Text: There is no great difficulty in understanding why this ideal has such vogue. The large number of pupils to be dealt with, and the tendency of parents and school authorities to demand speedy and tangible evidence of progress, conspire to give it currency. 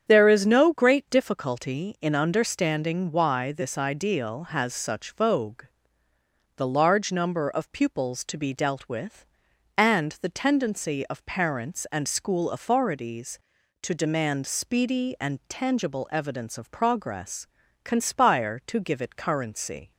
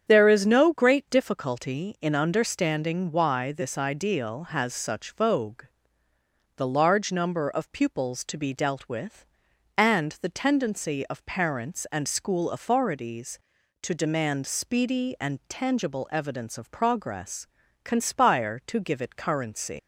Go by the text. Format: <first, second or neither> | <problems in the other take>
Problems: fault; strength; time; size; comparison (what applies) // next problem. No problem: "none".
first | starts louder than the rest; strong; until 1.0 s; 8 dB; strong in the first // leaves "currency" unfinished; at 19.7 s; 120 ms